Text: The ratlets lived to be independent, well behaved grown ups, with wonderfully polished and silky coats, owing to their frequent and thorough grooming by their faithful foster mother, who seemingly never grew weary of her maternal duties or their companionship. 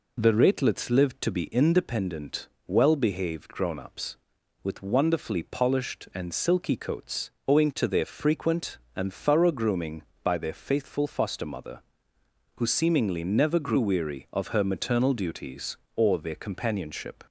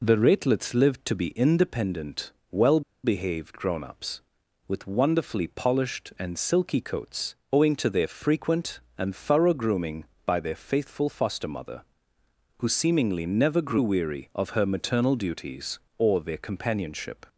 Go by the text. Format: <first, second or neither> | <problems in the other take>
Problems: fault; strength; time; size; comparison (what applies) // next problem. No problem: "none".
first | pauses between "well" and "behaved"; slight; at 2.8 s; 0.23 s long